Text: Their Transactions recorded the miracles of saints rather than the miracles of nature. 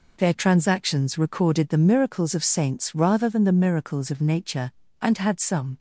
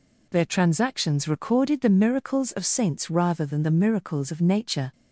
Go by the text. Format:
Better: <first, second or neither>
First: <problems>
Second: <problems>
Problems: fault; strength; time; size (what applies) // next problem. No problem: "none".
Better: second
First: goes on to say "And had some"; noticeable; from 5.0 s on; 0.78 s long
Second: none